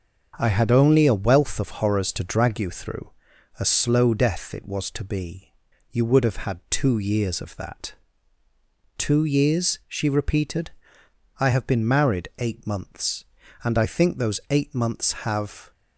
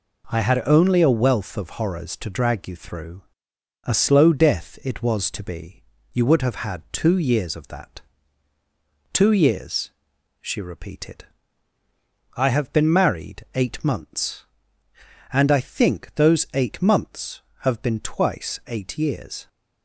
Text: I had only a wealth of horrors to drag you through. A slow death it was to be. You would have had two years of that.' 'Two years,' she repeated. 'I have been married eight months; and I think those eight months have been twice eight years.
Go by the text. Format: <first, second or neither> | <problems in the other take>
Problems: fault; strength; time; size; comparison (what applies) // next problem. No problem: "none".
second | starts louder than the rest; until 1.3 s; 7 dB // stops before "been twice eight years"; at 15.7 s